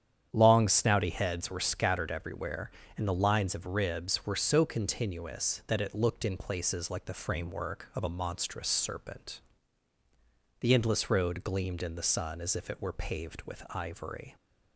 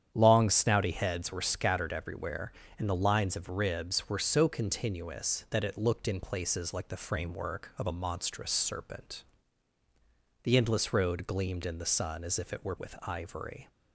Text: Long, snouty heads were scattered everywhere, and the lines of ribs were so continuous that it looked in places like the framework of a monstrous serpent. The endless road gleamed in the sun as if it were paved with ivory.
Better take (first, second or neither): first